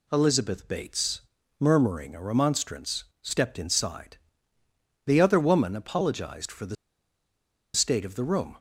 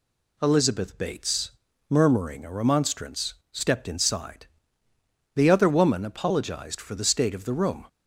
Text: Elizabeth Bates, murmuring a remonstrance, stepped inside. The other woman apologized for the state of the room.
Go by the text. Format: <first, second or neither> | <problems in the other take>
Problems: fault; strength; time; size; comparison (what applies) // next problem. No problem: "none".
second | pauses between "the" and "state"; at 6.7 s; 1.0 s long